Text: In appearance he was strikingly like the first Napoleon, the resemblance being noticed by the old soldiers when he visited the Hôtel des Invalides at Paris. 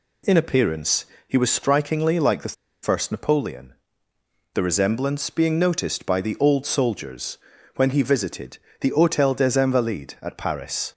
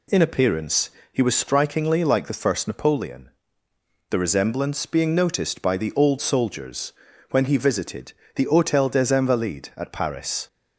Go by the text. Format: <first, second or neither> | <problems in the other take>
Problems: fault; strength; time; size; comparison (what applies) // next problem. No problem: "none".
second | pauses between "appearance" and "he"; slight; at 1.0 s; 0.22 s long; slight in the second // pauses between "the" and "first"; slight; at 2.5 s; 0.28 s long // pauses between "soldiers" and "when"; at 7.3 s; 0.38 s long; also in the second // pauses between "visited" and "the"; slight; at 8.5 s; 0.24 s long; slight in the second